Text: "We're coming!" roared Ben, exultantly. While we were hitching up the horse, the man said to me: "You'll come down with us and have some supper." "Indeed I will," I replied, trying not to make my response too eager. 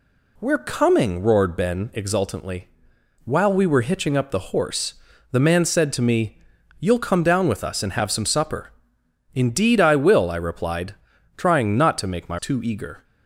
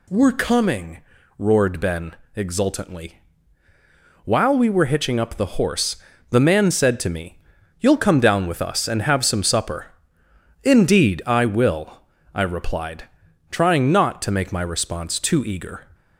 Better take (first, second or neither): second